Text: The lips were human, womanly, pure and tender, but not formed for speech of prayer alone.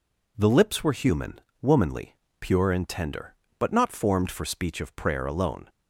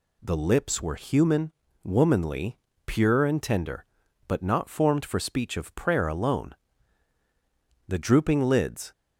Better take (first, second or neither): first